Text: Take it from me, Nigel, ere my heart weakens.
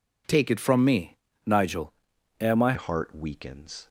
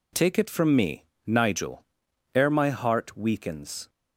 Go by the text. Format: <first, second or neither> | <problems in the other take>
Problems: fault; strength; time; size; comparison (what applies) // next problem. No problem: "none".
second | changes voice at "heart"; from 2.7 s on; 1.1 s long